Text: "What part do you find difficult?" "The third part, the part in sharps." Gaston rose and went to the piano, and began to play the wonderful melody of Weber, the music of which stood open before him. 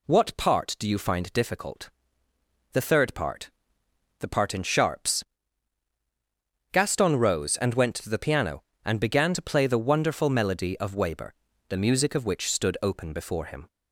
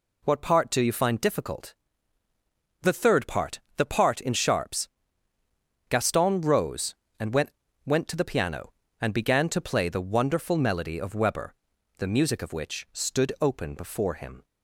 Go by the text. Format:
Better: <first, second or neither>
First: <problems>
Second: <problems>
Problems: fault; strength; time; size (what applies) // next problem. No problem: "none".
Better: first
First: none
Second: says "went" twice; at 7.8 s